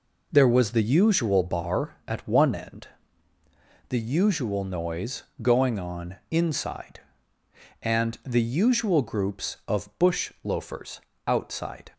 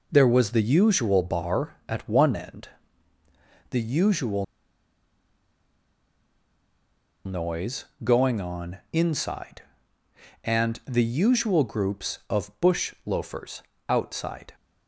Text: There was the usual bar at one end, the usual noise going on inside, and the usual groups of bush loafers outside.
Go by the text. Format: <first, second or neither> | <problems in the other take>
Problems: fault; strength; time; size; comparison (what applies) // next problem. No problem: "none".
first | pauses between "usual" and "noise"; strong; at 4.4 s; 2.8 s long // pauses between "noise" and "going"; slight; at 7.8 s; 0.18 s long; slight in the first // pauses between "loafers" and "outside"; slight; at 13.6 s; 0.24 s long; slight in the first